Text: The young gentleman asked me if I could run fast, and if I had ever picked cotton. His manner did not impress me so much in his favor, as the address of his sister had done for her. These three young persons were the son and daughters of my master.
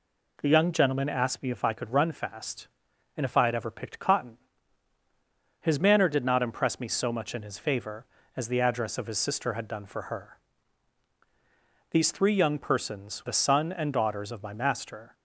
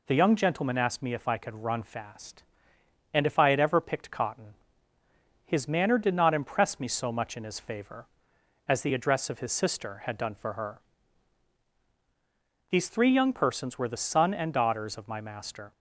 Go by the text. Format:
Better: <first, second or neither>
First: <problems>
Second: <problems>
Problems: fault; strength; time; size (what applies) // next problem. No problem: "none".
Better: second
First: skips "were"; at 13.2 s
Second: none